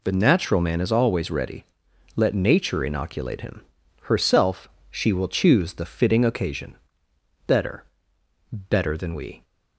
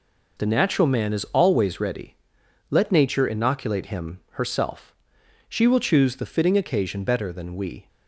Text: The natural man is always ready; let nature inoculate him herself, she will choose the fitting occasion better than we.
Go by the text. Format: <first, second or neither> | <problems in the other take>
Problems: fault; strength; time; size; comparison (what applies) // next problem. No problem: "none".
second | pauses between "him" and "herself"; at 3.6 s; 0.38 s long // pauses between "occasion" and "better"; noticeable; at 6.7 s; 0.72 s long // says "better" twice; at 8.5 s